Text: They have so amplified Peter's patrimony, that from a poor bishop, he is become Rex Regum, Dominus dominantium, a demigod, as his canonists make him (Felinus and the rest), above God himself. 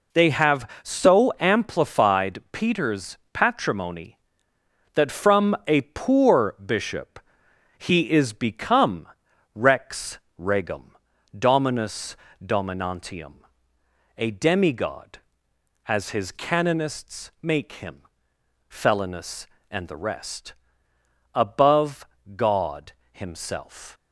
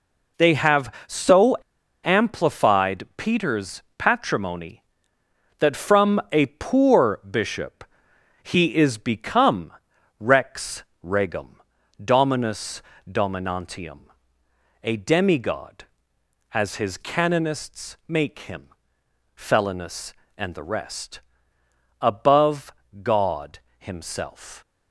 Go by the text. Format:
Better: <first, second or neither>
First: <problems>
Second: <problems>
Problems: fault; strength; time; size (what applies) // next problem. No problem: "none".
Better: first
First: pauses between "Peter's" and "patrimony"; slight; at 3.1 s; 0.16 s long // pauses between "become" and "Rex"; noticeable; at 9.0 s; 0.48 s long // pauses between "Rex" and "Regum"; slight; at 10.1 s; 0.18 s long // pauses between "Dominus" and "dominantium"; slight; at 12.1 s; 0.28 s long // pauses between "above" and "God"; slight; at 22.0 s; 0.30 s long // pauses between "God" and "himself"; slight; at 22.9 s; 0.20 s long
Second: pauses between "so" and "amplified"; noticeable; at 1.5 s; 0.47 s long // pauses between "Peter's" and "patrimony"; slight; at 3.8 s; 0.16 s long // pauses between "become" and "Rex"; noticeable; at 9.7 s; 0.48 s long // pauses between "Rex" and "Regum"; slight; at 10.8 s; 0.18 s long // pauses between "Dominus" and "dominantium"; slight; at 12.8 s; 0.28 s long // pauses between "above" and "God"; slight; at 22.7 s; 0.30 s long // pauses between "God" and "himself"; slight; at 23.5 s; 0.20 s long